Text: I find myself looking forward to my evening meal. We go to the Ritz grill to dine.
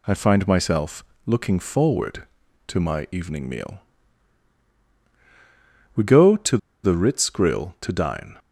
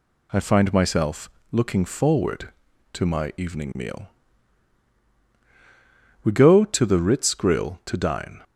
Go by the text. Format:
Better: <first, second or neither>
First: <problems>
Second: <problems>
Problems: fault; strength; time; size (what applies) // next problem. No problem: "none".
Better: second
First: pauses between "myself" and "looking"; slight; at 1.0 s; 0.22 s long // pauses between "to" and "the"; slight; at 6.5 s; 0.25 s long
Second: pauses between "myself" and "looking"; slight; at 1.2 s; 0.22 s long